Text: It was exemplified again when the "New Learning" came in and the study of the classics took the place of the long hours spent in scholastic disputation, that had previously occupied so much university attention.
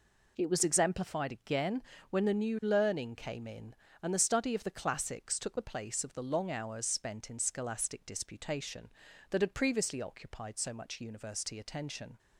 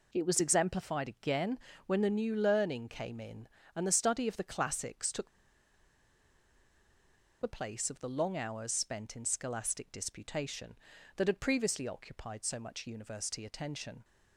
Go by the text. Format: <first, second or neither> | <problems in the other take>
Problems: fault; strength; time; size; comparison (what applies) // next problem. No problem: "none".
first | pauses between "again" and "when"; slight; at 1.5 s; 0.30 s long; slight in the first // pauses between "took" and "the"; strong; at 5.2 s; 2.1 s long